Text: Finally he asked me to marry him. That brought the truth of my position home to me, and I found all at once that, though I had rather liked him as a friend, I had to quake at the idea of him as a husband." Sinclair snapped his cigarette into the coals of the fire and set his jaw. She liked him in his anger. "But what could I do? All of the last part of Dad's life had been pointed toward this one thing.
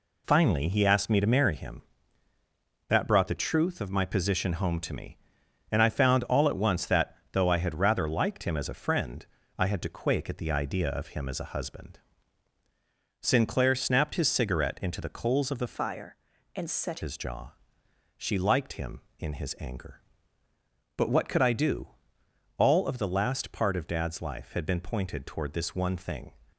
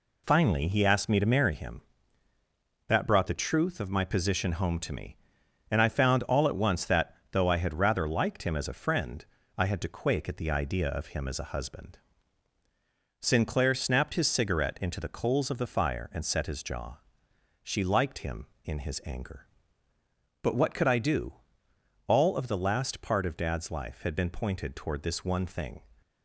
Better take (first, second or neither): second